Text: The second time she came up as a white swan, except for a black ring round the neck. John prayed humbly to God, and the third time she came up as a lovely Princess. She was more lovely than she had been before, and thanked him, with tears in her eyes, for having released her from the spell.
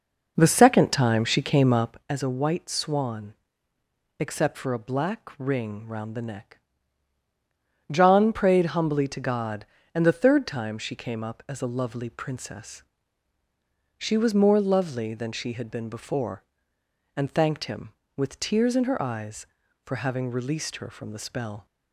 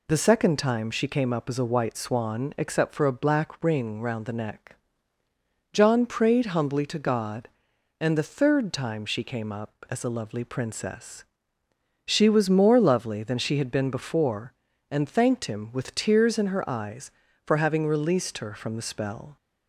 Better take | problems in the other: second | starts louder than the rest; noticeable; until 2.0 s; 5.5 dB

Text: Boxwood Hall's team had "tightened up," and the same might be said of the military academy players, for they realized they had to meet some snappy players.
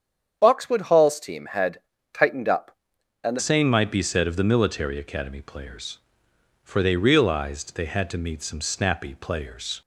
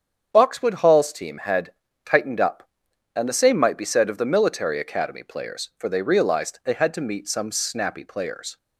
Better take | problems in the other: second | starts louder than the rest; strong; until 1.4 s; 8 dB; strong in the second // pauses between "had" and "tightened"; slight; at 1.7 s; 0.34 s long; slight in the second // changes voice at "same"; from 3.3 s on; 6.5 s long

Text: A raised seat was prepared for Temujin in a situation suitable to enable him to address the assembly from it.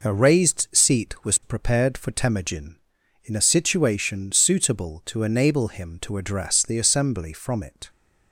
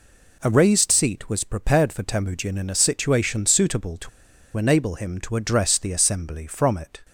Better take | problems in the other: first | pauses between "to" and "enable"; noticeable; at 4.0 s; 0.47 s long

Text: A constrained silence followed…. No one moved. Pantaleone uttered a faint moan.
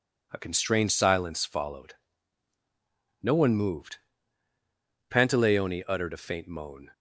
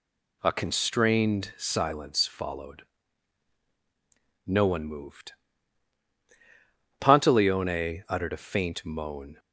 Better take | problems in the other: neither | none

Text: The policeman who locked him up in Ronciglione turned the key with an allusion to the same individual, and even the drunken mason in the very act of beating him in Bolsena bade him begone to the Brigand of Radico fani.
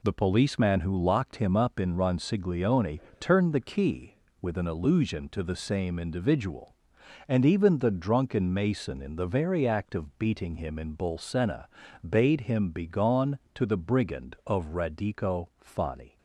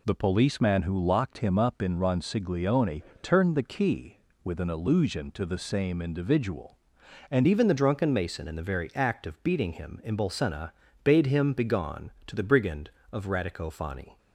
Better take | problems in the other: first | pauses between "Ronciglione" and "turned"; slight; at 3.0 s; 0.20 s long; slight in the first // changes voice at "even"; from 7.4 s on; 6.7 s long // pauses between "Bolsena" and "bade"; slight; at 10.7 s; 0.32 s long; also in the first

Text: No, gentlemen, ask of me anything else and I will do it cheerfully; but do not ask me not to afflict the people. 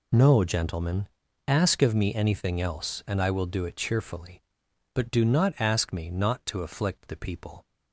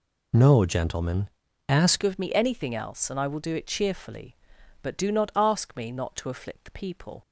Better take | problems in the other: first | changes voice at "of"; from 2.0 s on; 5.2 s long

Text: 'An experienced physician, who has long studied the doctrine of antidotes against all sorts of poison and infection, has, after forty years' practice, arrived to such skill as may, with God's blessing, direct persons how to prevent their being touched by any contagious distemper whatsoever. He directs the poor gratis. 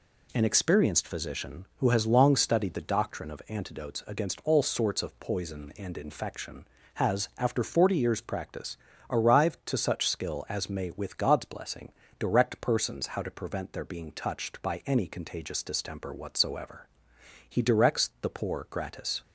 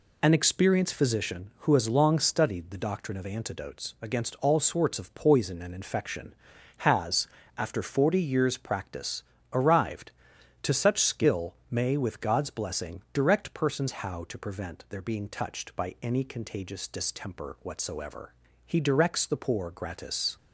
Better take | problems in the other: first | skips "as"; at 11.6 s

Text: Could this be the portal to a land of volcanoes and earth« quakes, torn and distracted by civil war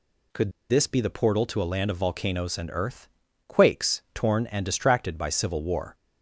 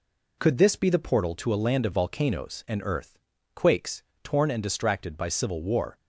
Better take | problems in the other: second | pauses between "Could" and "this"; slight; at 0.5 s; 0.19 s long // pauses between "earth" and "quakes"; at 3.0 s; 0.42 s long; also in the second

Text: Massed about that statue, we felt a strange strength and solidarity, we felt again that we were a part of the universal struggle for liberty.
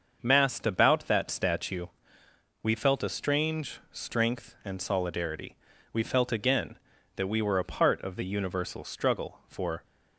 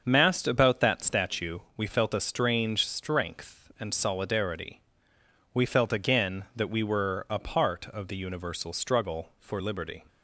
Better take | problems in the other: second | starts louder than the rest; until 1.2 s; 6.5 dB; also in the second // stops before "liberty"; at 9.8 s

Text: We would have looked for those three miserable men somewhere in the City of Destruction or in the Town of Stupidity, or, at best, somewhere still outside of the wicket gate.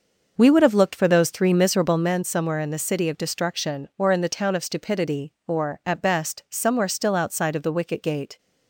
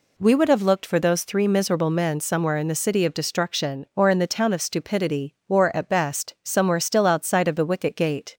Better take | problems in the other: second | starts louder than the rest; noticeable; until 2.2 s; 6 dB

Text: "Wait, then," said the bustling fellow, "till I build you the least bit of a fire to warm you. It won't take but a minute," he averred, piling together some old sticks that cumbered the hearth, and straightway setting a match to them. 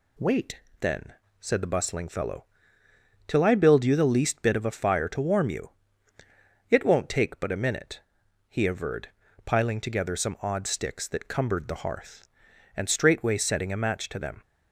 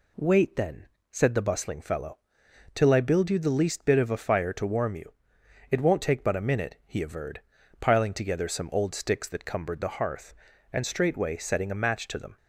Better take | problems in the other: second | says "odd" for "old"; at 10.4 s

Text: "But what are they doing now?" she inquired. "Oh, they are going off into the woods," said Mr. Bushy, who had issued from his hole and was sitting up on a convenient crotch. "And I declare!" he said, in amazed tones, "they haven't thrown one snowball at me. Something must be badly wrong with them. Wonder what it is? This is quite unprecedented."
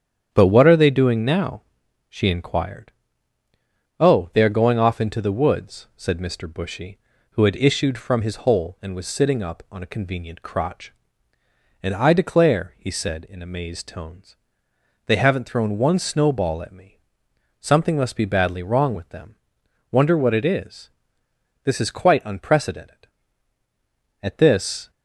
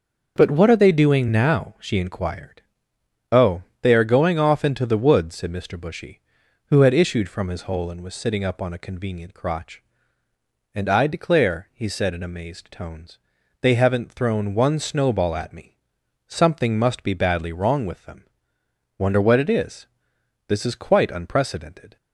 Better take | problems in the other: second | starts louder than the rest; strong; until 1.3 s; 9 dB; also in the second // goes on to say "At this"; noticeable; from 24.2 s on; 0.68 s long

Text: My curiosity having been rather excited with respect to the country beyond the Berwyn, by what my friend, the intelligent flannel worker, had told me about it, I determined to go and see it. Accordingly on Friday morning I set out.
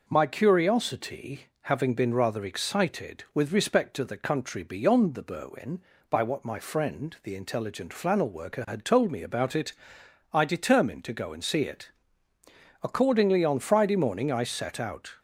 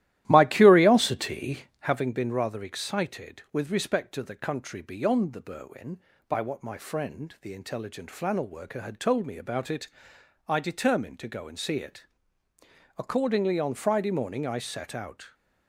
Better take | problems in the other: first | starts louder than the rest; strong; until 2.0 s; 14.5 dB // pauses between "curiosity" and "having"; slight; at 1.6 s; 0.16 s long; slight in the first

